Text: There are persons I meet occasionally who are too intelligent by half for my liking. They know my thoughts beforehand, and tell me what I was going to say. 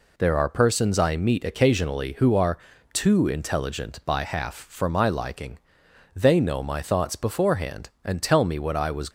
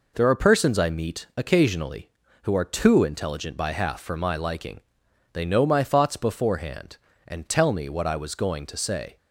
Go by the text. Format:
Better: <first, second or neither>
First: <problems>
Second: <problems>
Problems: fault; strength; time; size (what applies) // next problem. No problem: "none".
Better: second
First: pauses between "are" and "too"; slight; at 2.5 s; 0.36 s long // stops before "going to say"; at 9.0 s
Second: none